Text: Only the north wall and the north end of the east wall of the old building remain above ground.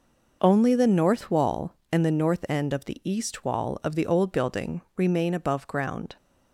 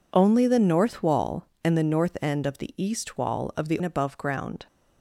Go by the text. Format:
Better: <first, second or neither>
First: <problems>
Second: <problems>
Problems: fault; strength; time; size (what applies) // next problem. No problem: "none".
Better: first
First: none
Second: skips "old building remain"; at 3.8 s